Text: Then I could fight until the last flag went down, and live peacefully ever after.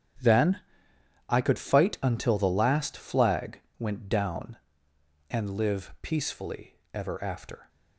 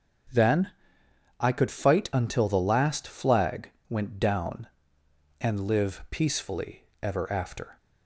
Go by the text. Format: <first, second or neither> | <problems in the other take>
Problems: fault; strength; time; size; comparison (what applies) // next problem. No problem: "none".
second | gets quieter; strong; throughout; 13 dB // starts louder than the rest; strong; until 1.9 s; 9.5 dB; strong in the second // pauses between "Then" and "I"; noticeable; at 0.5 s; 0.70 s long; noticeable in the second // pauses between "flag" and "went"; slight; at 3.5 s; 0.18 s long; slight in the second // pauses between "peacefully" and "ever"; slight; at 6.7 s; 0.18 s long; slight in the second